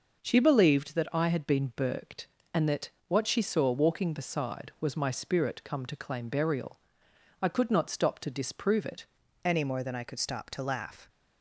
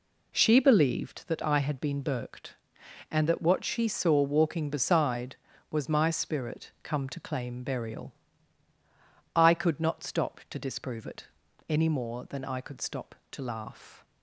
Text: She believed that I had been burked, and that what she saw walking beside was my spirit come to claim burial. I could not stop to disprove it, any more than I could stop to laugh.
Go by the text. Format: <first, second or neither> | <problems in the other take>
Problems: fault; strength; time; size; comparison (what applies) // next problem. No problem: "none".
second | pauses between "that" and "what"; slight; at 2.9 s; 0.16 s long // changes voice at "any"; from 9.4 s on; 1.6 s long